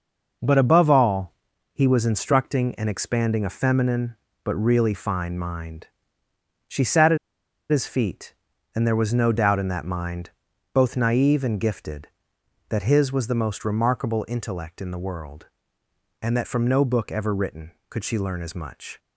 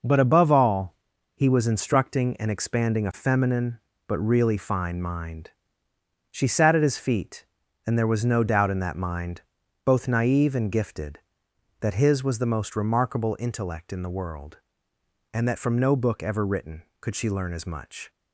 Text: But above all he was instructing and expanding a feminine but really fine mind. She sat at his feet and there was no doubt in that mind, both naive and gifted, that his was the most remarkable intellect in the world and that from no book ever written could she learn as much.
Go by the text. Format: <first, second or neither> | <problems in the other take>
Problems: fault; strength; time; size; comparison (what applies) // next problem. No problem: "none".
second | pauses between "all" and "he"; at 1.3 s; 0.40 s long; also in the second // pauses between "at" and "his"; noticeable; at 7.1 s; 0.52 s long